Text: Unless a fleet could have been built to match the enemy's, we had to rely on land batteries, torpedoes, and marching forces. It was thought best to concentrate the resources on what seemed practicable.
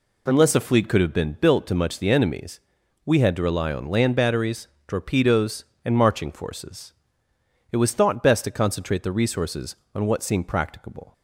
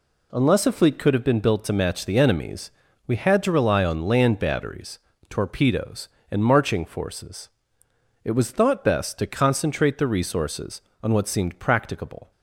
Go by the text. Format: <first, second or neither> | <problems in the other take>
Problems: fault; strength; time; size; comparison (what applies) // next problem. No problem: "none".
second | says "much" for "match"; at 1.7 s